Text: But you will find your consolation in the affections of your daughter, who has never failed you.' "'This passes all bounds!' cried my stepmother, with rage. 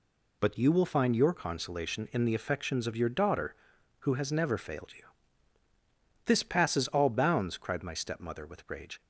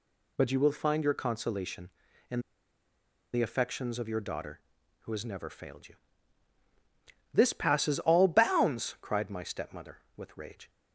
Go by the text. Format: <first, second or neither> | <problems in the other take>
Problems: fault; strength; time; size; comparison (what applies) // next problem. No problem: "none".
first | pauses between "in" and "the"; noticeable; at 2.3 s; 0.93 s long